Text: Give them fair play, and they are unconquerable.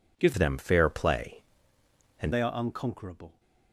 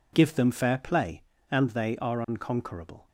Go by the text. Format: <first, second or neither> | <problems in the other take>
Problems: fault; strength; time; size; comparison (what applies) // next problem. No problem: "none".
second | changes voice from "them" to "and"; from 0.3 to 2.3 s; 2.0 s long